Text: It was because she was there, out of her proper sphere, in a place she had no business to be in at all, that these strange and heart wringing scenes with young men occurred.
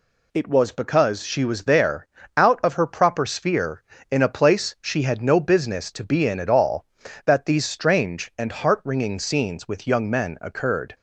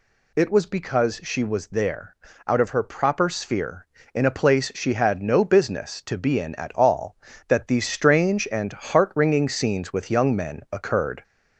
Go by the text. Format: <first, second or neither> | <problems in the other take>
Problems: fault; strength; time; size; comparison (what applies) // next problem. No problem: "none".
first | gets louder; slight; throughout; 2.5 dB